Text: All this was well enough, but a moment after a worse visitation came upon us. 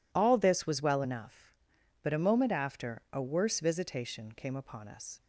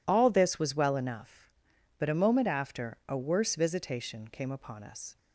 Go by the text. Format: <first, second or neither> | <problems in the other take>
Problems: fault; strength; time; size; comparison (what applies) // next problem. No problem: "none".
neither | none